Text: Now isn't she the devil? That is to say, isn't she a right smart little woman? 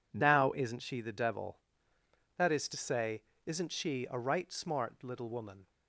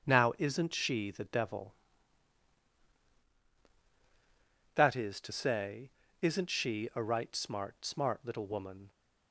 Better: first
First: none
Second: starts louder than the rest; strong; until 1.1 s; 7 dB // says "smart" twice; at 7.8 s

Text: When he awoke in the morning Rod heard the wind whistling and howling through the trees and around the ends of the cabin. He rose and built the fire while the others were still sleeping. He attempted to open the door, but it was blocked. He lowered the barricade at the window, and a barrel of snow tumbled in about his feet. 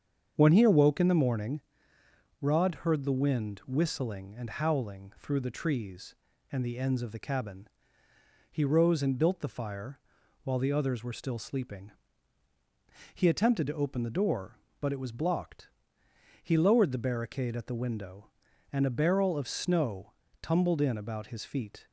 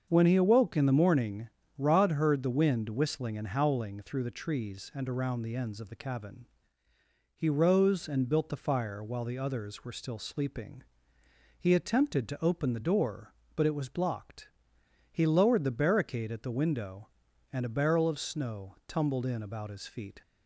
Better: second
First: starts louder than the rest; strong; until 1.3 s; 7 dB // pauses between "morning" and "Rod"; noticeable; at 1.6 s; 0.80 s long // skips "around"; at 6.6 s // pauses between "fire" and "while"; noticeable; at 9.9 s; 0.46 s long // pauses between "snow" and "tumbled"; slight; at 20.1 s; 0.29 s long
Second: starts louder than the rest; until 1.1 s; 7 dB // pauses between "morning" and "Rod"; slight; at 1.4 s; 0.28 s long

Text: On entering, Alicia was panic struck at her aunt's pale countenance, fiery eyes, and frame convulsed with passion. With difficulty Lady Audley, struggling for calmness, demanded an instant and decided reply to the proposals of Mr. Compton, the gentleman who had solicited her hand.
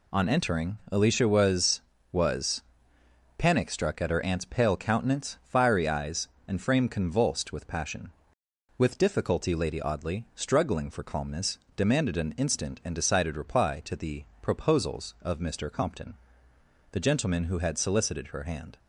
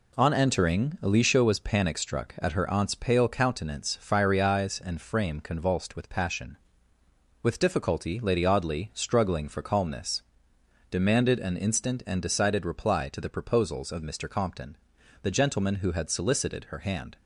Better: second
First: says "was" twice; at 2.1 s // pauses between "the" and "proposals"; slight; at 14.2 s; 0.16 s long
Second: none

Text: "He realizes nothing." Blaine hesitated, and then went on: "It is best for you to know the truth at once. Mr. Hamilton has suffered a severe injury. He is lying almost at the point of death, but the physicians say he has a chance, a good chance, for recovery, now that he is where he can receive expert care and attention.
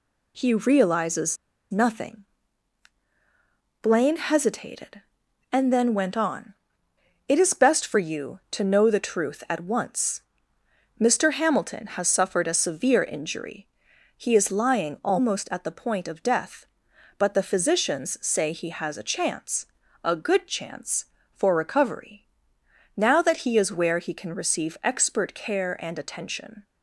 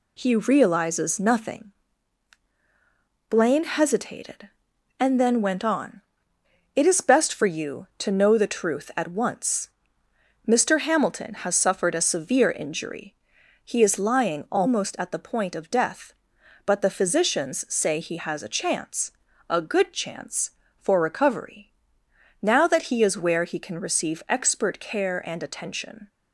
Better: second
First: pauses between "realizes" and "nothing"; slight; at 1.3 s; 0.35 s long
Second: none

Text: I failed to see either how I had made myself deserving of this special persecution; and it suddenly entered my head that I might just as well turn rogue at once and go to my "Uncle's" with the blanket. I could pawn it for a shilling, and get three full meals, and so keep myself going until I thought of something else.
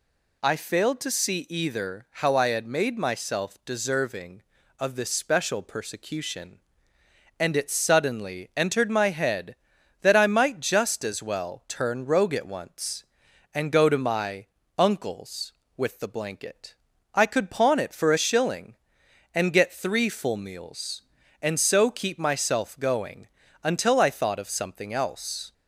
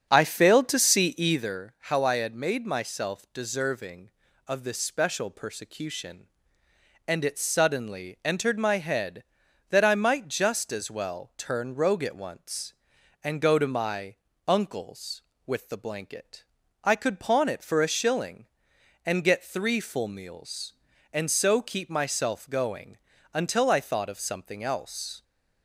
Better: first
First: pauses between "my" and "Uncle's"; slight; at 14.4 s; 0.32 s long // pauses between "going" and "until"; slight; at 23.2 s; 0.34 s long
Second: starts louder than the rest; strong; until 1.5 s; 7.5 dB // pauses between "my" and "Uncle's"; slight; at 14.1 s; 0.32 s long // pauses between "going" and "until"; slight; at 22.9 s; 0.34 s long

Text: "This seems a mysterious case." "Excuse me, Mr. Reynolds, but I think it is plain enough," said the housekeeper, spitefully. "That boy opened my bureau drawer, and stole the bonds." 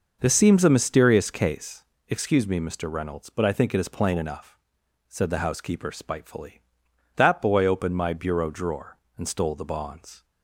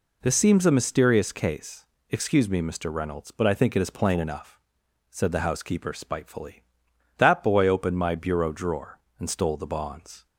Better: second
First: starts louder than the rest; noticeable; until 2.0 s; 6 dB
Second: none

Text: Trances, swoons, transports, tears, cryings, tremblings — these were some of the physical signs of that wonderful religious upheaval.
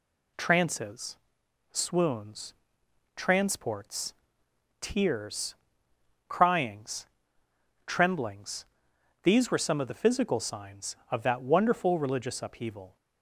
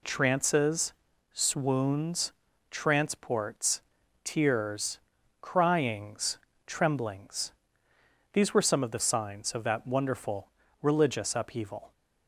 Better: first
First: none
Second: skips "physical"; at 8.9 s // pauses between "wonderful" and "religious"; slight; at 10.4 s; 0.34 s long

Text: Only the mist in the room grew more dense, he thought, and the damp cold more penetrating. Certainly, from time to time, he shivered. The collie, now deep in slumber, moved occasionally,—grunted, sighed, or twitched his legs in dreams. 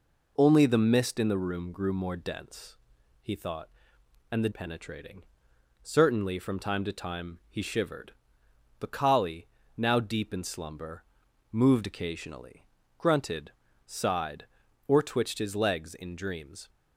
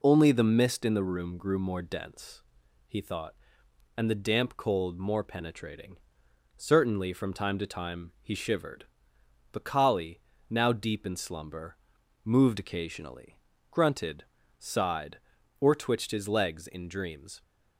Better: second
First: skips "damp cold more"; at 4.5 s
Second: none

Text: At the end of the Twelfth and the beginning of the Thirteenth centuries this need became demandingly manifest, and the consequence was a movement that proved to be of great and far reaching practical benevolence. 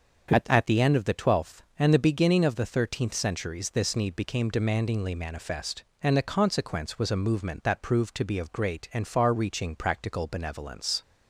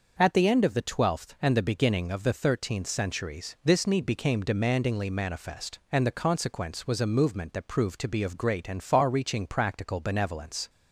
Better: second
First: starts louder than the rest; until 1.3 s; 6.5 dB // says "At" twice; at 0.4 s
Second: starts louder than the rest; noticeable; until 1.2 s; 6 dB

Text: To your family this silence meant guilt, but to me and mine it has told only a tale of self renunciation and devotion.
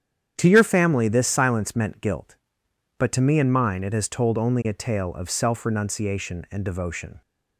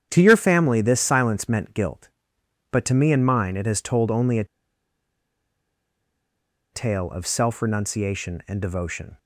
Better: first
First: starts louder than the rest; strong; until 1.3 s; 9 dB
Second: starts louder than the rest; strong; until 1.1 s; 9 dB // pauses between "a" and "tale"; strong; at 4.4 s; 2.2 s long

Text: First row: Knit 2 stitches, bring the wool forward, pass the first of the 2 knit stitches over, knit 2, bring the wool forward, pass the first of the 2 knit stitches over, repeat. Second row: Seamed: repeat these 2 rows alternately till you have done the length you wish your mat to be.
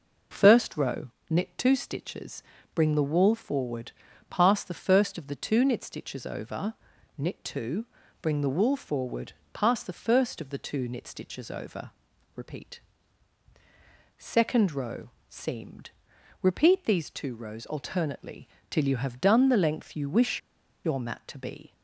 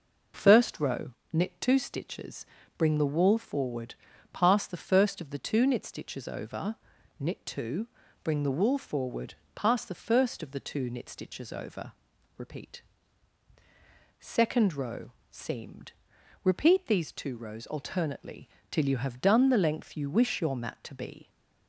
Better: second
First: pauses between "alternately" and "till"; slight; at 18.4 s; 0.20 s long // pauses between "wish" and "your"; at 20.3 s; 0.44 s long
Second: pauses between "alternately" and "till"; slight; at 18.4 s; 0.20 s long

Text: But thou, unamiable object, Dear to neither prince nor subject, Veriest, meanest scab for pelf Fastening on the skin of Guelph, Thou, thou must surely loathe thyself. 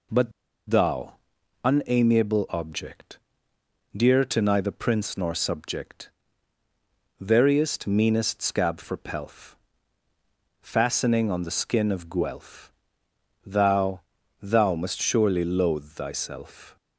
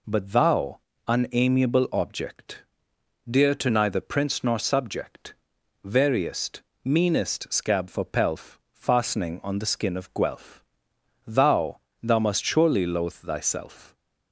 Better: second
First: pauses between "But" and "thou"; at 0.3 s; 0.38 s long // pauses between "pelf" and "Fastening"; at 9.5 s; 1.0 s long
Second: none

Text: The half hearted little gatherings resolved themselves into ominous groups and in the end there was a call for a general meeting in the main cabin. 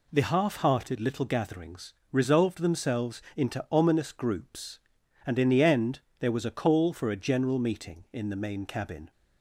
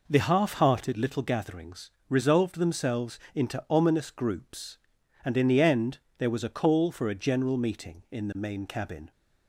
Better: first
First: pauses between "gatherings" and "resolved"; slight; at 1.9 s; 0.20 s long // pauses between "end" and "there"; slight; at 5.9 s; 0.22 s long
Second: starts louder than the rest; noticeable; until 1.1 s; 4.5 dB // pauses between "gatherings" and "resolved"; slight; at 1.8 s; 0.20 s long // pauses between "themselves" and "into"; slight; at 3.1 s; 0.16 s long // pauses between "end" and "there"; slight; at 5.9 s; 0.22 s long

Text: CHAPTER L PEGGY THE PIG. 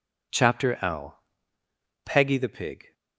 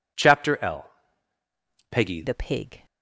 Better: first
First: pauses between "L" and "PEGGY"; noticeable; at 1.1 s; 0.87 s long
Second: pauses between "L" and "PEGGY"; at 0.8 s; 1.0 s long // changes voice at "THE"; from 2.2 s on; 0.6 s long

